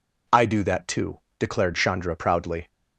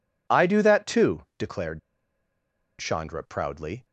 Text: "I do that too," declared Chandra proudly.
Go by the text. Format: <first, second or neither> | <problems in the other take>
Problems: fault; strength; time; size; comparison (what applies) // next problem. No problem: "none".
first | pauses between "declared" and "Chandra"; at 1.7 s; 0.99 s long